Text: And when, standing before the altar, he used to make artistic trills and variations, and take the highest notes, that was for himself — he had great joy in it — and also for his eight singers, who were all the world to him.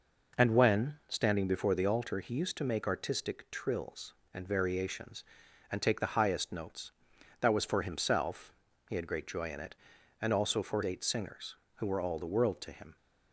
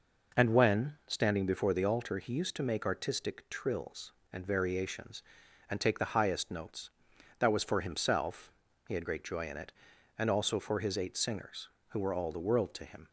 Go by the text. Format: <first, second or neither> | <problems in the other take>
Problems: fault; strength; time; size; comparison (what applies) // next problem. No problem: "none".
second | skips "his"; at 10.8 s